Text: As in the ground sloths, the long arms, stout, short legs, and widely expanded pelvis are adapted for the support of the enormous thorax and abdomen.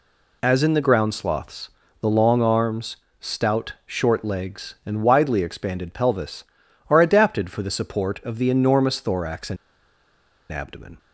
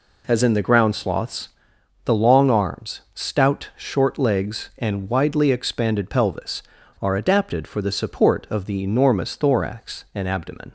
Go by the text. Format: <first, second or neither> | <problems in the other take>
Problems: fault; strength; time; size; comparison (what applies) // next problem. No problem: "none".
second | pauses between "and" and "abdomen"; noticeable; at 9.5 s; 0.96 s long